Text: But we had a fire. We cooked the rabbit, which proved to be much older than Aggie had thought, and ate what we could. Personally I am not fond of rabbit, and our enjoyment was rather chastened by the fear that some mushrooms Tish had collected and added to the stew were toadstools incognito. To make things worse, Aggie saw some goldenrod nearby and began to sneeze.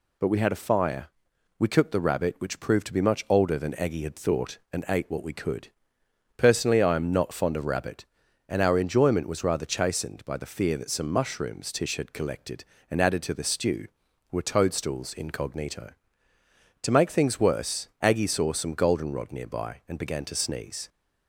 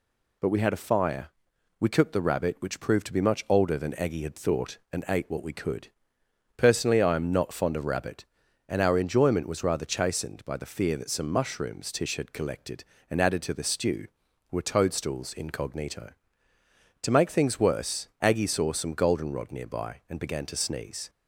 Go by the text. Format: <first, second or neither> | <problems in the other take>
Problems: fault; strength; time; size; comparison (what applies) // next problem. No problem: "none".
neither | none